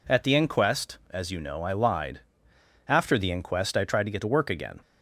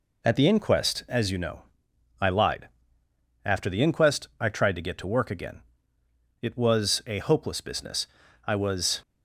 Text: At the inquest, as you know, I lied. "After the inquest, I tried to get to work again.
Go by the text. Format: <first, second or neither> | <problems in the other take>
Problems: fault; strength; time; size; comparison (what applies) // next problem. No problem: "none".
first | goes on to say "It was a hopeless business I was"; strong; from 6.4 s on; 2.6 s long